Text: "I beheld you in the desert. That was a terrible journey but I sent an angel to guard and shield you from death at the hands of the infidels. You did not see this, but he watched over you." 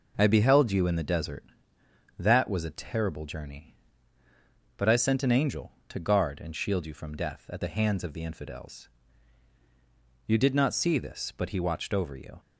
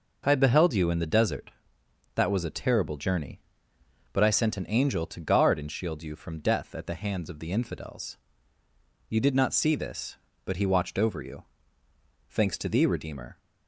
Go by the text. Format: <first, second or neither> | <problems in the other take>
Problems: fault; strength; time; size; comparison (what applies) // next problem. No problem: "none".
first | goes on to say "Thanks to thee Redeemer"; noticeable; from 12.2 s on; 1.1 s long